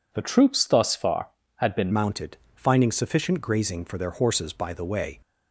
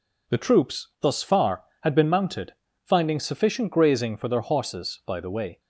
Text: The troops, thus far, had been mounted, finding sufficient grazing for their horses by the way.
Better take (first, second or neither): second